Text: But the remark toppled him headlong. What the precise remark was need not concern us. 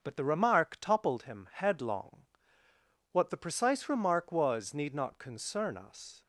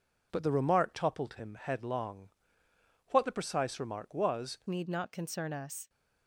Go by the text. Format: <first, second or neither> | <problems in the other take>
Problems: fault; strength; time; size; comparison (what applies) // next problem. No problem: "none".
first | changes voice at "need"; from 4.6 s on; 1.2 s long